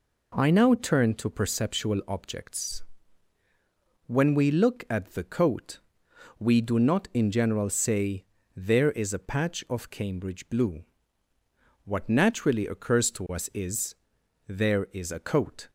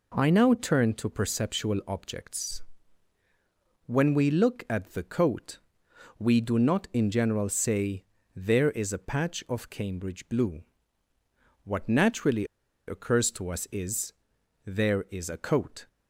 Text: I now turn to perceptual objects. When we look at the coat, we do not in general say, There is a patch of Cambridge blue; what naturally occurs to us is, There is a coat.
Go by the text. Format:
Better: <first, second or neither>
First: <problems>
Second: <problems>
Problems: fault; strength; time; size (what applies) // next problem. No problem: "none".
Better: first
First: none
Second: pauses between "naturally" and "occurs"; at 12.4 s; 0.42 s long